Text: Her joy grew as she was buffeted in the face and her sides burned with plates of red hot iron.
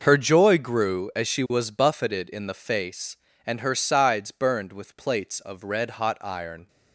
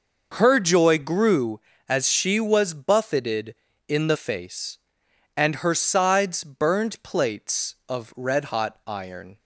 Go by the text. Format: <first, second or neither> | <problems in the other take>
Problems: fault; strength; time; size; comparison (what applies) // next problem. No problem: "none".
first | skips "with"; at 7.0 s